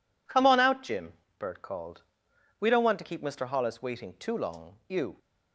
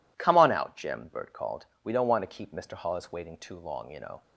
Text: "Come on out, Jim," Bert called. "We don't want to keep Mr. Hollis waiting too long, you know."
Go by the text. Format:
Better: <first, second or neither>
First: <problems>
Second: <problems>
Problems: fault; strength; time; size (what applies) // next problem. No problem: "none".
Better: second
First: stops before "know"; at 5.1 s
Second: none